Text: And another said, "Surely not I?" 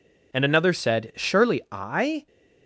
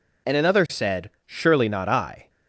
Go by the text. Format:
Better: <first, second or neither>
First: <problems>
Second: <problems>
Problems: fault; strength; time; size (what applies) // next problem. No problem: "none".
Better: second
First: skips "not"; at 1.6 s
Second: none